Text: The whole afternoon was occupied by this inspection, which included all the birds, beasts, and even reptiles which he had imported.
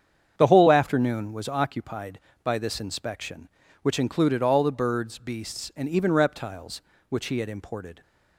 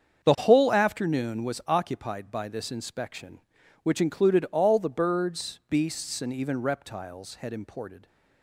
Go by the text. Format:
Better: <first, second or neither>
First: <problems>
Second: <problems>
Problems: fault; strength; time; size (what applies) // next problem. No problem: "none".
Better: first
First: starts louder than the rest; strong; until 1.4 s; 7.5 dB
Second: starts louder than the rest; strong; until 1.2 s; 7 dB // skips "which he"; at 7.3 s